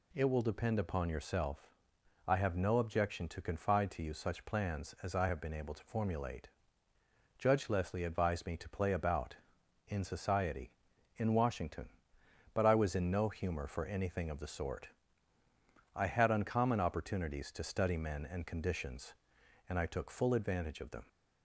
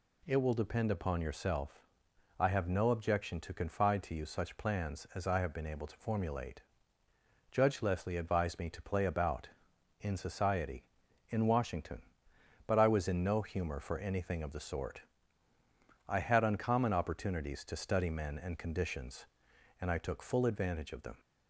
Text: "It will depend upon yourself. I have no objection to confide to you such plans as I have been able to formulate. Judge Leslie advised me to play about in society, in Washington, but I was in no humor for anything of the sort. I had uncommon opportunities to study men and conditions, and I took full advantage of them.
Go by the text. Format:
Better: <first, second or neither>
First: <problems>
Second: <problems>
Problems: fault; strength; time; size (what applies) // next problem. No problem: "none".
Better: neither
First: none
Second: none